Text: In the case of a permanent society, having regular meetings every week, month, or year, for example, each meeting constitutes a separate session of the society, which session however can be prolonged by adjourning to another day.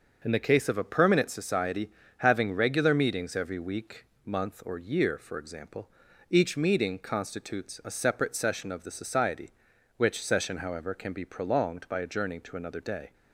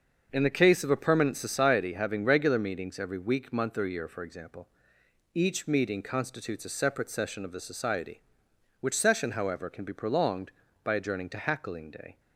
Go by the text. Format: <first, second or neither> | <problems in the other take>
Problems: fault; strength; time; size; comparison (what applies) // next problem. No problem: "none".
first | starts louder than the rest; until 1.3 s; 6.5 dB; noticeable in the first // says "hackling" for "another"; at 11.3 s